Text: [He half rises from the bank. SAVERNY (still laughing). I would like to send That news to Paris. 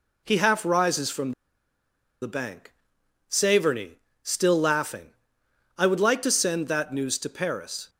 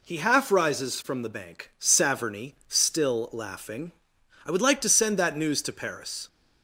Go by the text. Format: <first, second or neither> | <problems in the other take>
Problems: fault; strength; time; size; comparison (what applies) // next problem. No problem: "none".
second | pauses between "from" and "the"; noticeable; at 1.3 s; 0.90 s long